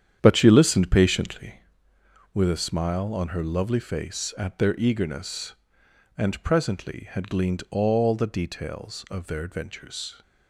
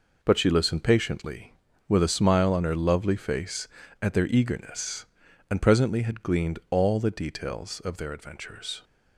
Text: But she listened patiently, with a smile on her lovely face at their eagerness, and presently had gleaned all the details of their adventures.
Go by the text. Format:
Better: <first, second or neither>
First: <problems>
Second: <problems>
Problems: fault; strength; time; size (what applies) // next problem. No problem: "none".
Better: second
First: starts louder than the rest; strong; until 1.7 s; 9 dB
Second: none